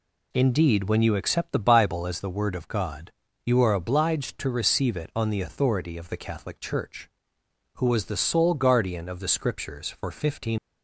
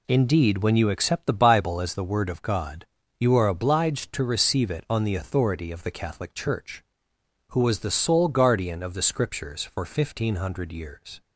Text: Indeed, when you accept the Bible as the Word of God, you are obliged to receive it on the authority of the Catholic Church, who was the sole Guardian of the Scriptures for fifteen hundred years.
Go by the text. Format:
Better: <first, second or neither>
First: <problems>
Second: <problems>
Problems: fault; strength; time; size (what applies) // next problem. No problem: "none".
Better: second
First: stops before "hundred years"; at 10.5 s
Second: none